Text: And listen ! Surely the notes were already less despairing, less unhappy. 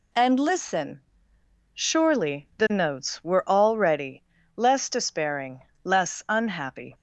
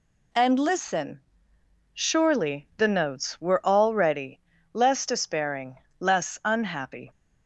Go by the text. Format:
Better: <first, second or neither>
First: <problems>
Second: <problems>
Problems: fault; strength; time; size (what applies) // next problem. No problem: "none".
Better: neither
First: pauses between "already" and "less"; slight; at 4.2 s; 0.32 s long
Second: pauses between "already" and "less"; slight; at 4.3 s; 0.32 s long